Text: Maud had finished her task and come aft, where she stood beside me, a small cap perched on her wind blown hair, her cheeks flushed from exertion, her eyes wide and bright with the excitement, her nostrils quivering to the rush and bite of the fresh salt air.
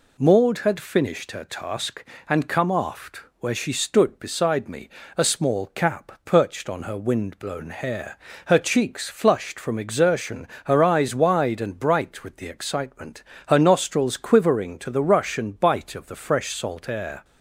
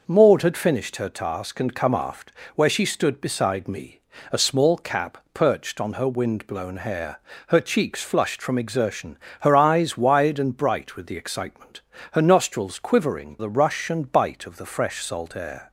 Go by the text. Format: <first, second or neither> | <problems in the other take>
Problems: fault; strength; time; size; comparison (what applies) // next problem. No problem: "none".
first | pauses between "cap" and "perched"; slight; at 5.1 s; 0.16 s long // skips "to"; at 13.3 s